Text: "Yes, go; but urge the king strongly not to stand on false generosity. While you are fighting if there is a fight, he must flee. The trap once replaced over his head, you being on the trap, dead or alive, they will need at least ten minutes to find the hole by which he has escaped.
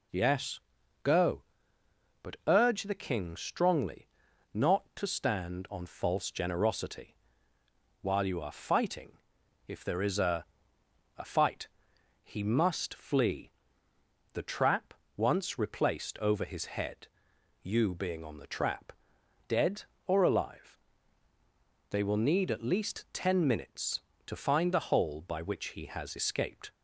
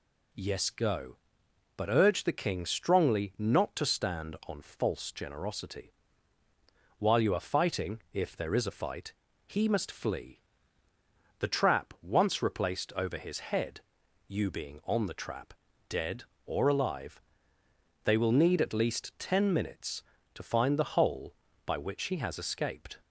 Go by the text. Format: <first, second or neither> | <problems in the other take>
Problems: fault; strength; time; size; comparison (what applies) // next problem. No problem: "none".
second | pauses between "strongly" and "not"; noticeable; at 4.0 s; 0.46 s long // pauses between "fighting" and "if"; noticeable; at 9.1 s; 0.50 s long // says "a" twice; at 11.1 s // pauses between "trap" and "once"; slight; at 14.9 s; 0.22 s long